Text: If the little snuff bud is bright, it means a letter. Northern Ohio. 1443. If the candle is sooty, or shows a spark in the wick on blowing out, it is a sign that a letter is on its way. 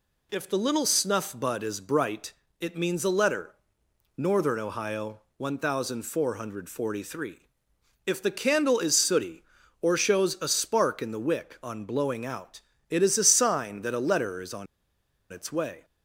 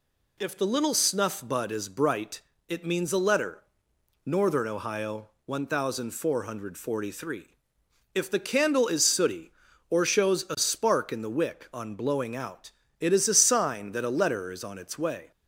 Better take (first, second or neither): second